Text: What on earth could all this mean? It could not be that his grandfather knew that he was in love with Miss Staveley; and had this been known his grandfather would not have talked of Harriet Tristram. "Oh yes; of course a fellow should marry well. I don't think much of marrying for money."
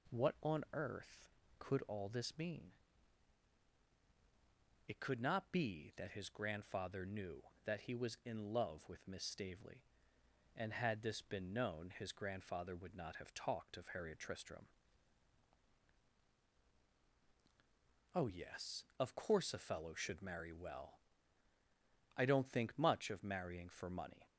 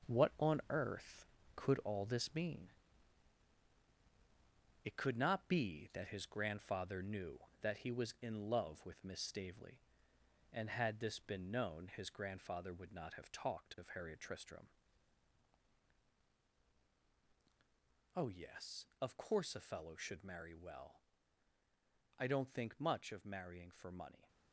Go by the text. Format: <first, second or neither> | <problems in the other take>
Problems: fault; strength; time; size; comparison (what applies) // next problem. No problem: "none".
first | gets quieter; strong; throughout; 7.5 dB